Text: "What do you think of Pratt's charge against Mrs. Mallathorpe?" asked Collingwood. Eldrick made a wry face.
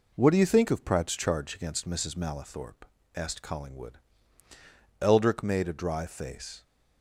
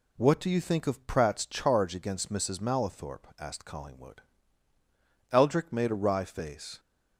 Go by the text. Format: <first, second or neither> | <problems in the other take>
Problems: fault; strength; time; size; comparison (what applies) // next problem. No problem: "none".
second | says "dry" for "wry"; at 5.7 s